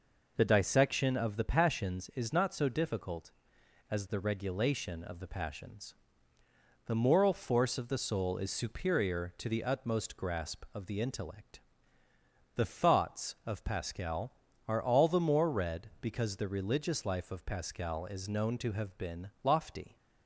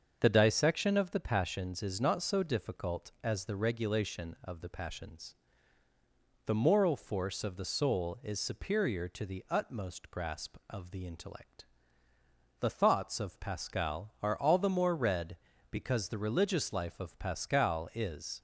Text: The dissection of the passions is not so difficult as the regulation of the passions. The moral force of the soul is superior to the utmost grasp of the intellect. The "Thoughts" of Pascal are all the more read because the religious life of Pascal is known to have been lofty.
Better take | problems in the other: first | starts louder than the rest; until 1.2 s; 6.5 dB // stops before "known to have been lofty"; at 18.3 s

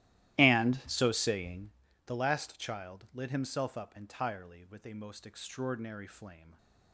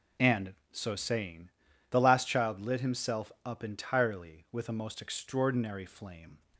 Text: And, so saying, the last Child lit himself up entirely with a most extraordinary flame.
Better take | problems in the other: second | starts louder than the rest; strong; until 1.7 s; 15 dB

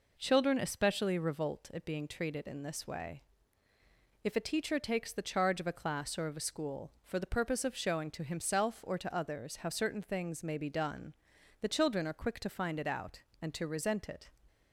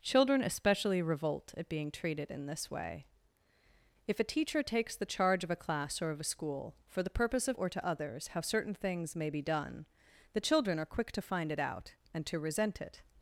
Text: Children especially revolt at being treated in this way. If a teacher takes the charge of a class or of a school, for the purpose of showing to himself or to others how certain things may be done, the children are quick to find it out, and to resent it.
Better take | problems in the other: first | skips "showing to himself"; at 7.5 s

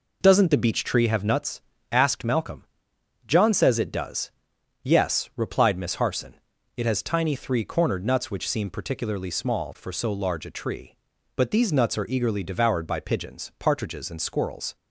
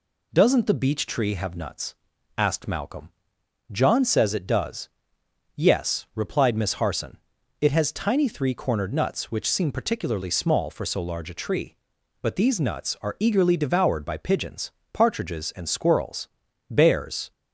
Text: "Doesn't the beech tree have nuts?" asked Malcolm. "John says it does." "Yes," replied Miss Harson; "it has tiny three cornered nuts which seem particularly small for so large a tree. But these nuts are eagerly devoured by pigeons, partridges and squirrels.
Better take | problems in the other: first | goes on to say "Bears"; noticeable; from 16.6 s on; 0.62 s long

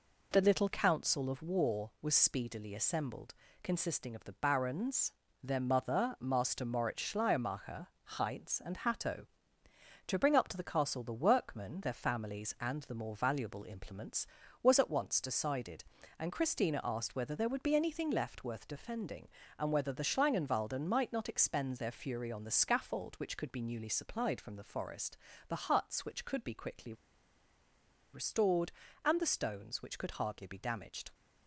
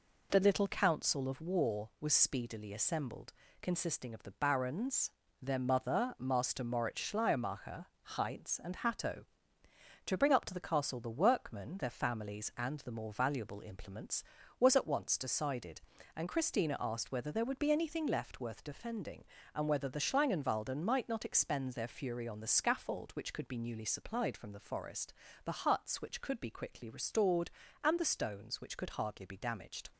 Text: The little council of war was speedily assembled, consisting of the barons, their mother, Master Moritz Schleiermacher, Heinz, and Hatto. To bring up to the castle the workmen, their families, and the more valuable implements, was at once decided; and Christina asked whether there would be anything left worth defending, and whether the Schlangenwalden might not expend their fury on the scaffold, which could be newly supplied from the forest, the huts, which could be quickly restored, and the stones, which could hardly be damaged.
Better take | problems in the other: second | pauses between "quickly" and "restored"; at 26.9 s; 1.1 s long

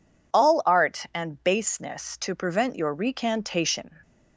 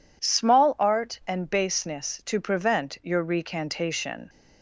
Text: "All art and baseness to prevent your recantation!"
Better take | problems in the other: first | says "Small" for "All"; at 0.2 s

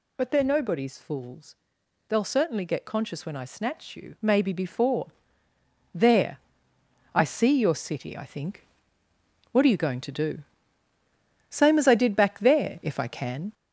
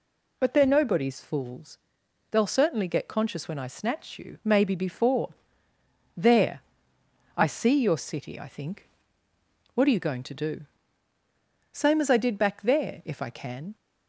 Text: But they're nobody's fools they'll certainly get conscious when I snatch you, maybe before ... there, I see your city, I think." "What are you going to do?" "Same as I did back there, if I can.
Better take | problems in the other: second | gets louder; noticeable; throughout; 4.5 dB // pauses between "fools" and "they'll"; noticeable; at 1.5 s; 0.52 s long; noticeable in the second

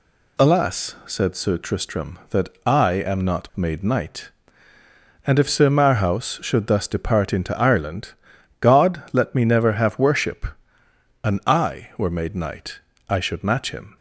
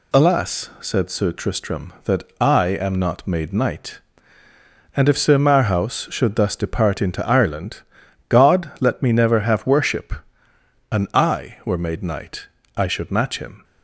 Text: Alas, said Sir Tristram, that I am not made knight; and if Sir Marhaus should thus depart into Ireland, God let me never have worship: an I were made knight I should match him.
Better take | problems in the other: neither | pauses between "knight" and "I"; slight; the same in both

